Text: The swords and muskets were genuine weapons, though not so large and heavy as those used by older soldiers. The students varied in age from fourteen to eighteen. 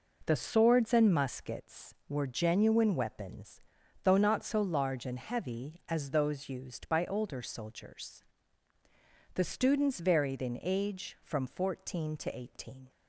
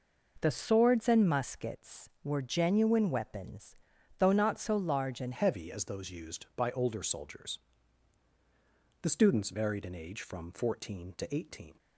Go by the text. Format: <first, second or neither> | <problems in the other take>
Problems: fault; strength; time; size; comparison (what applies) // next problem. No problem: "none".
first | changes voice at "heavy"; from 5.3 s on; 6.4 s long